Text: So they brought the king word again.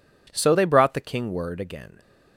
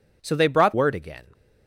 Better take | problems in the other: first | skips "the king"; at 0.7 s

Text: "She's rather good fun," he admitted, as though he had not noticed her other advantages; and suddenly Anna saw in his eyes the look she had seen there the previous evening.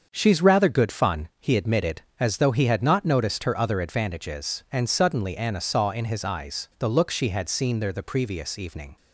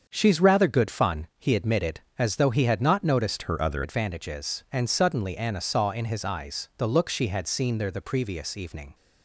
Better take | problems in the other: first | starts louder than the rest; until 1.0 s; 7 dB; also in the first // changes voice from "her" to "other"; from 3.4 to 3.8 s; 0.4 s long

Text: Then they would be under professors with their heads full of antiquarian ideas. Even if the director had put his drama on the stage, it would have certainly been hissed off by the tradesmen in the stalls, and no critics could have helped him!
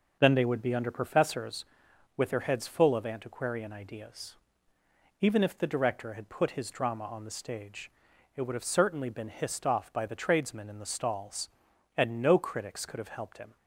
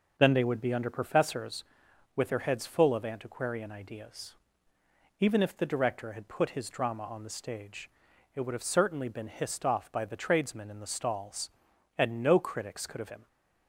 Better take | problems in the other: first | skips "helped"; at 13.1 s

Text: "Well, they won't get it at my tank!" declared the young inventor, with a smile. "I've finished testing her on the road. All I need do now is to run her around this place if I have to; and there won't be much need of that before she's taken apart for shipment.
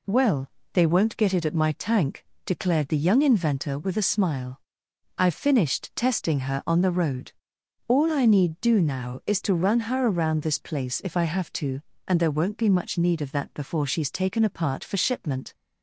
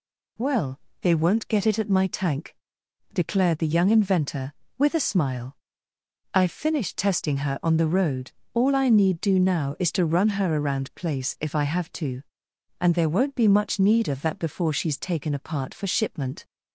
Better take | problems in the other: first | skips "this"; at 10.9 s

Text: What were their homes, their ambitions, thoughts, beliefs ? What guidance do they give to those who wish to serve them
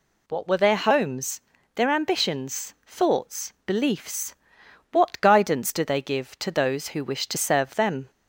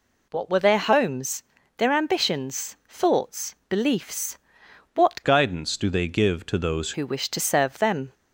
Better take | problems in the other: first | changes voice from "guidance" to "those"; from 5.2 to 6.9 s; 1.7 s long

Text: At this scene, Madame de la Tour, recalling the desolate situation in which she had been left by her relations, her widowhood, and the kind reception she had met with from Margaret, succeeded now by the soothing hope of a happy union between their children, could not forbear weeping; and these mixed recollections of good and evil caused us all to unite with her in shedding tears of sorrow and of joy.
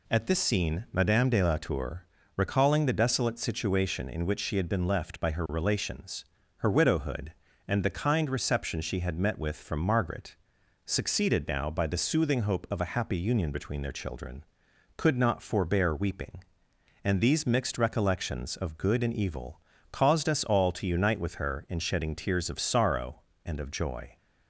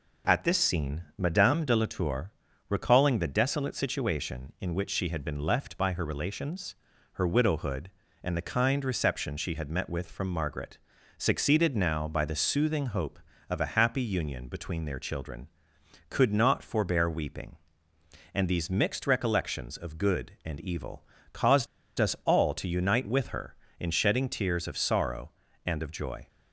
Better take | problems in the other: first | pauses between "evil" and "caused"; slight; at 21.0 s; 0.28 s long; slight in the first // pauses between "caused" and "us"; slight; at 21.6 s; 0.32 s long

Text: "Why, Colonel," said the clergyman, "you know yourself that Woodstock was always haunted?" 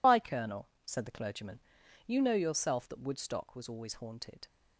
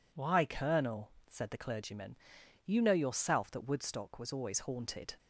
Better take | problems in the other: second | loses the start of "Why"; at 0.0 s; 60 ms

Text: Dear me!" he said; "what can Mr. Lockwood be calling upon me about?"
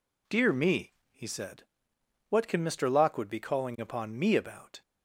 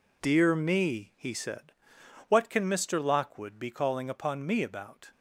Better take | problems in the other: neither | none

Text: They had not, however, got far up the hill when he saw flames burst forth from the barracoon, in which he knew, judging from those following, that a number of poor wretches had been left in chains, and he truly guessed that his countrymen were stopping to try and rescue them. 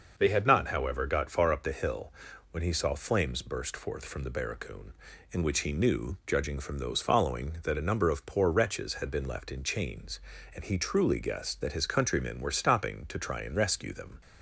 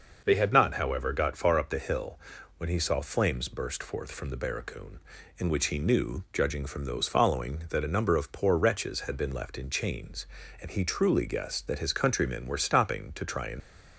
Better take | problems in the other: first | pauses between "hill" and "when"; at 2.1 s; 0.38 s long; also in the first // stops before "rescue them"; at 13.6 s

